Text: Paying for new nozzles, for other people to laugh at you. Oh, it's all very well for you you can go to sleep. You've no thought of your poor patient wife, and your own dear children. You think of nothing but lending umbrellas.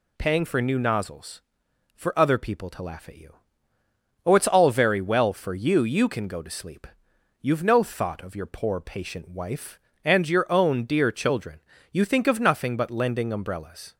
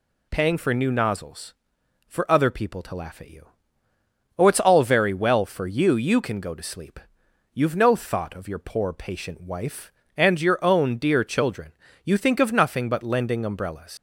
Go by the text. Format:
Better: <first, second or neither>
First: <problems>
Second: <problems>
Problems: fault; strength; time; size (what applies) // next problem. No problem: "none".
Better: first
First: none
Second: leaves "umbrellas" unfinished; at 13.9 s; 110 ms